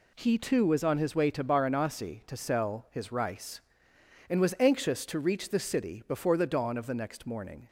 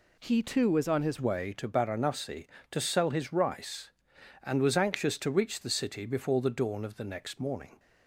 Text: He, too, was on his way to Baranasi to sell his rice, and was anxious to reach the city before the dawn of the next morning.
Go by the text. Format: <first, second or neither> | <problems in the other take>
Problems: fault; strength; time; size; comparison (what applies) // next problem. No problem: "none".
first | changes voice at "way"; from 1.1 s on; 6.6 s long